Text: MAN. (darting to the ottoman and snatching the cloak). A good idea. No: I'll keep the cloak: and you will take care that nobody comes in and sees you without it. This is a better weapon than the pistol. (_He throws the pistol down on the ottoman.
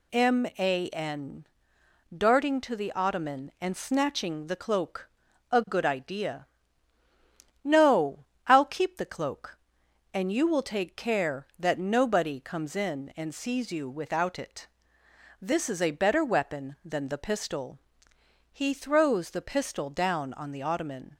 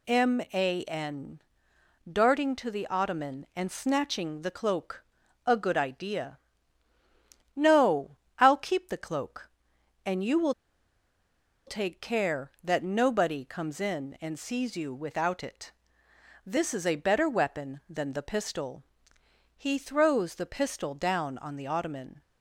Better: first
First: none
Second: pauses between "will" and "take"; at 10.5 s; 1.1 s long

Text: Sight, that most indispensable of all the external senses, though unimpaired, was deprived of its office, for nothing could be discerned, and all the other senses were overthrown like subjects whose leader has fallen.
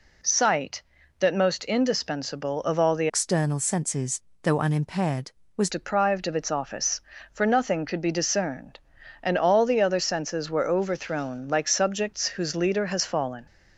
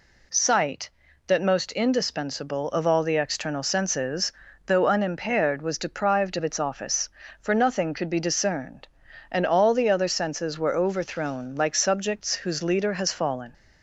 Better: second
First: changes voice from "external" to "was"; from 3.0 to 5.6 s; 2.6 s long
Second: none

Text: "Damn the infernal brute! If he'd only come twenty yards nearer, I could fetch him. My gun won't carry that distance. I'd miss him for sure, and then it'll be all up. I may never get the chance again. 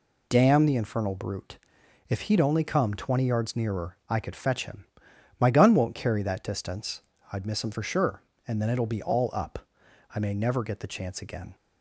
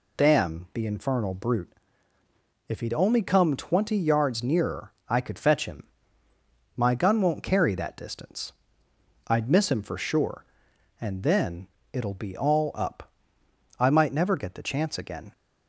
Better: first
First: none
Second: pauses between "then" and "it'll"; slight; at 11.6 s; 0.24 s long // says "might" for "may"; at 13.8 s

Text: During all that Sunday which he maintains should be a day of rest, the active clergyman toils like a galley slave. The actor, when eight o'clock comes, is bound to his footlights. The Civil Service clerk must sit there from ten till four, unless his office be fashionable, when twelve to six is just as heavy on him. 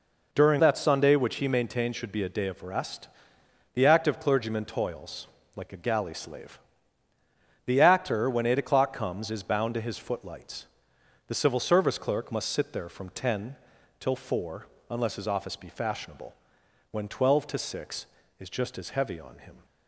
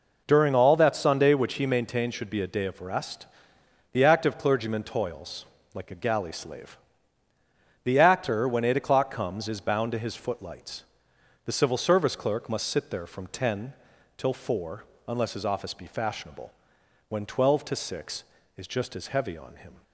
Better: second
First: skips "all"; at 0.5 s // pauses between "toils" and "like"; slight; at 5.2 s; 0.28 s long // pauses between "ten" and "till"; at 13.5 s; 0.44 s long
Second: pauses between "toils" and "like"; slight; at 5.4 s; 0.28 s long // pauses between "ten" and "till"; at 13.7 s; 0.44 s long

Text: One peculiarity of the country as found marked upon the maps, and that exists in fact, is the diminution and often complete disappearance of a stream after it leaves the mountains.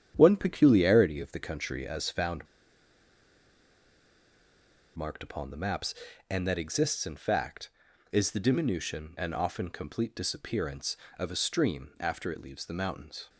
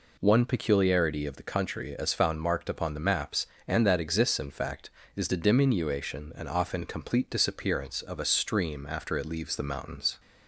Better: second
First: starts louder than the rest; strong; until 1.1 s; 9 dB // pauses between "found" and "marked"; strong; at 2.4 s; 2.5 s long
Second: none

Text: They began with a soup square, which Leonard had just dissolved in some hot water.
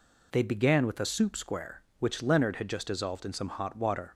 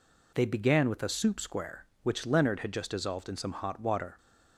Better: neither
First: none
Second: none

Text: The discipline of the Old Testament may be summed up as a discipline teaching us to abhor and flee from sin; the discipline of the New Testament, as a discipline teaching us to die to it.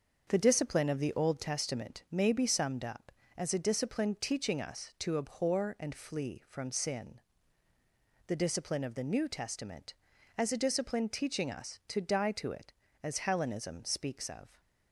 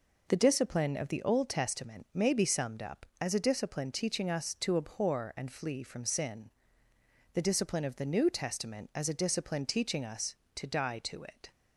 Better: second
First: starts louder than the rest; until 1.2 s; 6.5 dB // goes on to say "As Hellenism speaks of"; from 13.0 s on; 1.5 s long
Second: none

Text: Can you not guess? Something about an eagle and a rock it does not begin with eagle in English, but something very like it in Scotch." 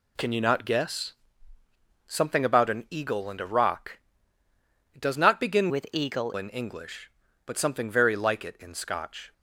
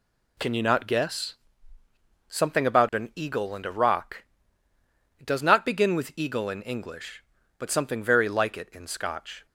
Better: second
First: pauses between "rock" and "it"; noticeable; at 3.9 s; 0.96 s long // changes voice from "with" to "eagle"; from 5.6 to 6.3 s; 0.7 s long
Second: pauses between "rock" and "it"; noticeable; at 4.2 s; 0.96 s long

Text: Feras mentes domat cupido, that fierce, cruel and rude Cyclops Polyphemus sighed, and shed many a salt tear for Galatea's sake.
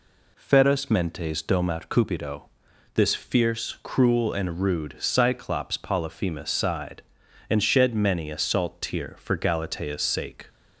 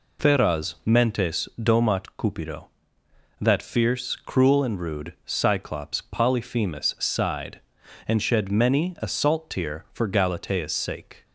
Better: second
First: says "this" for "that"; at 2.9 s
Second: none

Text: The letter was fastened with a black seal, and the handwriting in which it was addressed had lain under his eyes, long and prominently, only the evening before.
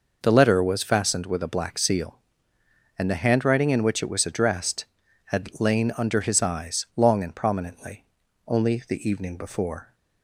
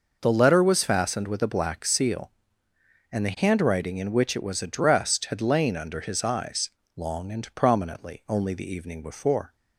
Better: neither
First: none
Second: none

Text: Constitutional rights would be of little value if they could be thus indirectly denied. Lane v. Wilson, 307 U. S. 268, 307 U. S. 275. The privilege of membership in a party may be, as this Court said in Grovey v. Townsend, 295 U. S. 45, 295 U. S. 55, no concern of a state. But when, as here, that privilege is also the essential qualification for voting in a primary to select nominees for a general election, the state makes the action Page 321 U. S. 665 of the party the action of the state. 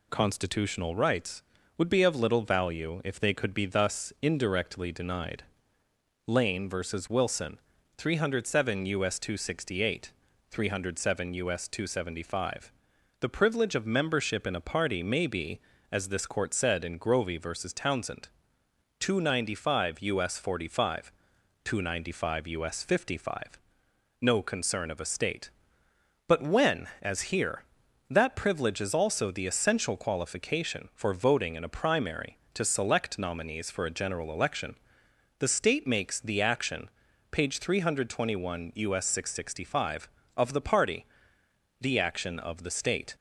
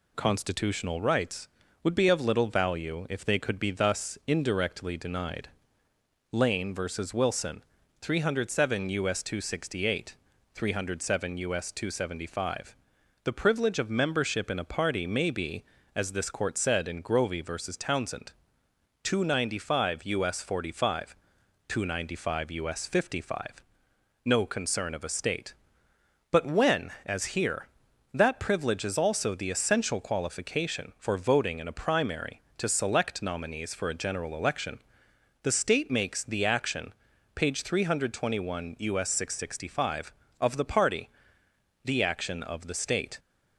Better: neither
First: pauses between "action" and "Page"; at 36.8 s; 0.42 s long // pauses between "party" and "the"; noticeable; at 41.0 s; 0.74 s long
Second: pauses between "action" and "Page"; at 36.9 s; 0.42 s long // pauses between "party" and "the"; noticeable; at 41.0 s; 0.74 s long

